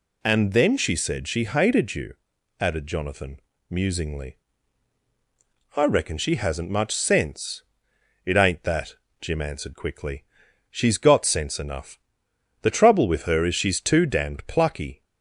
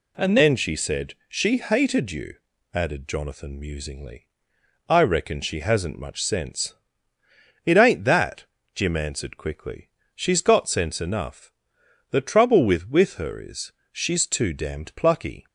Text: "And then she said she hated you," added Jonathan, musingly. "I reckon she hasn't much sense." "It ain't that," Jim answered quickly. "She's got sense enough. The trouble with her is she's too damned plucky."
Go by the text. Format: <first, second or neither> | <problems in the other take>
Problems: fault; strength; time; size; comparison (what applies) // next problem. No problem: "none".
first | says "with" twice; at 12.8 s // pauses between "is" and "she's"; slight; at 13.7 s; 0.20 s long